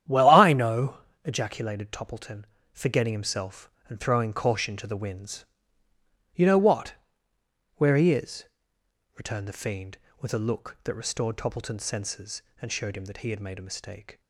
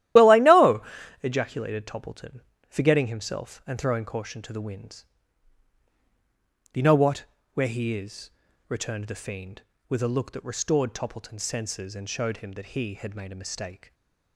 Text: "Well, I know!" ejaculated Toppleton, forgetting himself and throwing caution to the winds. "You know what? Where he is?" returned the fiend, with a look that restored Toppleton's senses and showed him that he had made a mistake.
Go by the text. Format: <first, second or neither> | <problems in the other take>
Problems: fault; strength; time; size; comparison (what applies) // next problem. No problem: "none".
first | loses the start of "Well"; at 0.1 s; 40 ms // starts louder than the rest; strong; until 1.5 s; 13.5 dB; strong in the first // stays silent after the last word; slight; from 13.8 s on; 0.5 s long